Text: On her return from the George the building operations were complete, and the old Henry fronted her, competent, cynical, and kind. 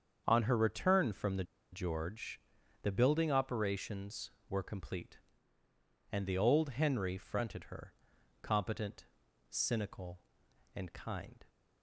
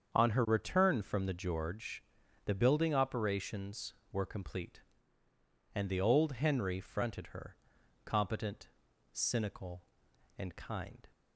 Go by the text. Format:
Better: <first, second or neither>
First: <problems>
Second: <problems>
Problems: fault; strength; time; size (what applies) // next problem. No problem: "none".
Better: second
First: starts louder than the rest; strong; until 1.2 s; 7 dB // pauses between "the" and "George"; slight; at 1.4 s; 0.28 s long // pauses between "George" and "the"; at 2.4 s; 0.42 s long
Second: starts louder than the rest; strong; until 1.1 s; 7 dB // pauses between "George" and "the"; at 2.0 s; 0.42 s long